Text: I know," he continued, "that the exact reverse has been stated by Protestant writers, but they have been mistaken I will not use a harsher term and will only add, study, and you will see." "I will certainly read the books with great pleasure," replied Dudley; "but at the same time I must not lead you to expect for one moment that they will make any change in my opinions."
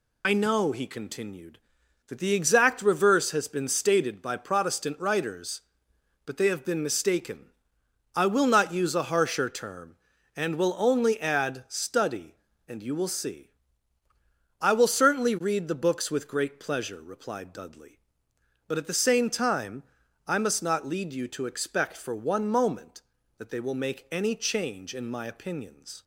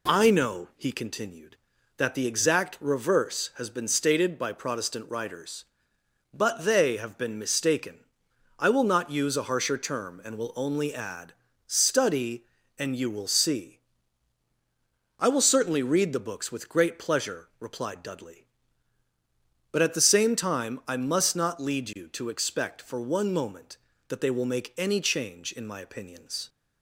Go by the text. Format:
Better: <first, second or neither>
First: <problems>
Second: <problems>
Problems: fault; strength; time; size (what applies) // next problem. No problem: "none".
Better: second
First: loses the start of "I"; at 0.2 s; 50 ms // pauses between "mistaken" and "I"; noticeable; at 7.5 s; 0.66 s long // pauses between "time" and "I"; at 19.8 s; 0.44 s long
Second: pauses between "mistaken" and "I"; noticeable; at 8.0 s; 0.56 s long